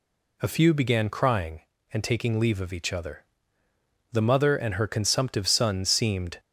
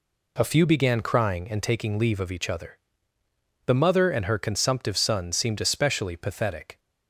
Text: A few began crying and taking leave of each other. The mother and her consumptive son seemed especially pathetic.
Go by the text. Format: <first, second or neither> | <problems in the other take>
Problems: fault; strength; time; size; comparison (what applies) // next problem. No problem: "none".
second | stops before "especially pathetic"; at 6.3 s